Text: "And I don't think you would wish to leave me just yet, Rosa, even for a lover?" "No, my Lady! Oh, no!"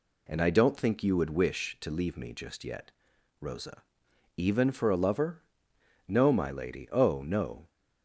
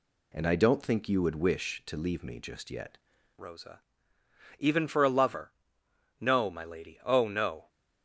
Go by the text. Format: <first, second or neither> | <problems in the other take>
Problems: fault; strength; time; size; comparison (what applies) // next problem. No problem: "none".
first | changes voice at "Rosa"; from 3.3 s on; 4.3 s long